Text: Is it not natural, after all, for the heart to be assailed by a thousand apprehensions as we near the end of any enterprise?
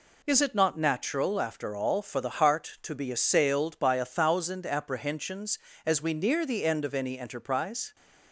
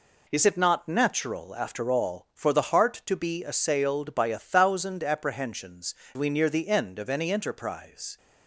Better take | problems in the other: first | skips "as"; at 6.0 s

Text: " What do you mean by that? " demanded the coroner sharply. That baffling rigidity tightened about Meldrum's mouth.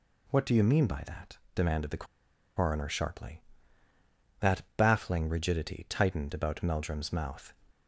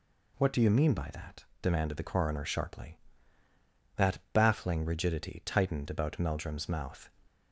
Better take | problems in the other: second | pauses between "the" and "coroner"; noticeable; at 2.0 s; 0.52 s long // pauses between "That" and "baffling"; slight; at 4.6 s; 0.16 s long; slight in the second

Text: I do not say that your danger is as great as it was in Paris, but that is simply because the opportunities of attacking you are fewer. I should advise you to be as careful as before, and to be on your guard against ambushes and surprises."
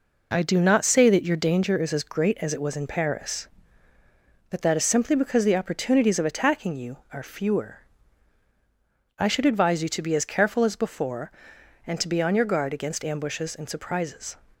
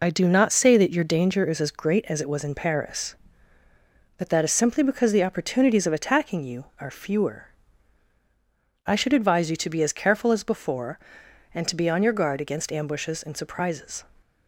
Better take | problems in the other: first | loses the start of "I"; at 0.0 s; 30 ms

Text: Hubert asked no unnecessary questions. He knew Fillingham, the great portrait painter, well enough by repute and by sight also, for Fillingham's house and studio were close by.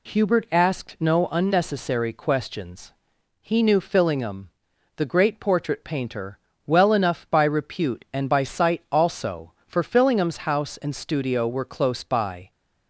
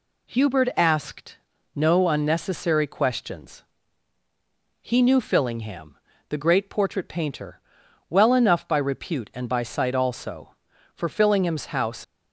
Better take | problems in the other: first | pauses between "asked" and "no"; slight; at 1.3 s; 0.36 s long // stops before "and studio were close by"; at 12.0 s

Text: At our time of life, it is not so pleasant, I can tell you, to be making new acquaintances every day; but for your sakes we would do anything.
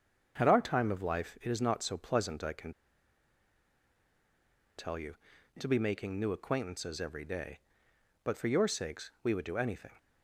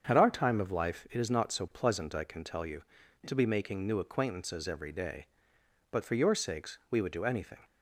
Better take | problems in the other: second | starts louder than the rest; strong; until 1.3 s; 7 dB; strong in the second // pauses between "can" and "tell"; strong; at 2.7 s; 2.0 s long

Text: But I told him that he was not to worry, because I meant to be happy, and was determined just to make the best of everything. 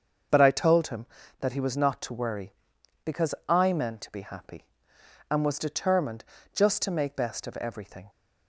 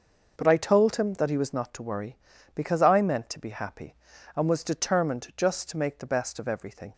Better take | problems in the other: second | starts louder than the rest; until 1.6 s; 6.5 dB // pauses between "determined" and "just"; slight; at 6.2 s; 0.30 s long // skips "the"; at 7.1 s

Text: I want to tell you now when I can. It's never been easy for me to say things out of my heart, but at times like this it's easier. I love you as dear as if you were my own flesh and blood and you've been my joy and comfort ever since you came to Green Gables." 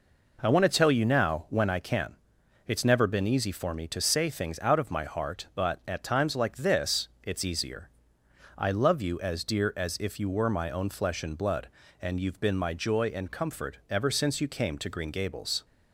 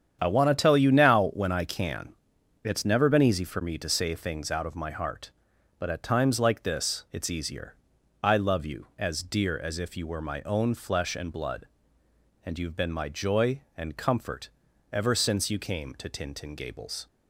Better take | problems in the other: first | starts louder than the rest; strong; until 1.2 s; 8.5 dB // pauses between "comfort" and "ever"; at 14.5 s; 0.42 s long // says "Tintin" for "Green"; at 16.0 s

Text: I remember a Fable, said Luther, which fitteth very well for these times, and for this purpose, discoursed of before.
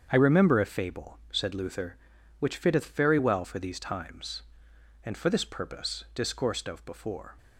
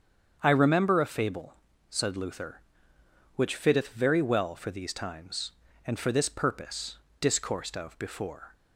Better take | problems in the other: neither | starts louder than the rest; strong; the same in both

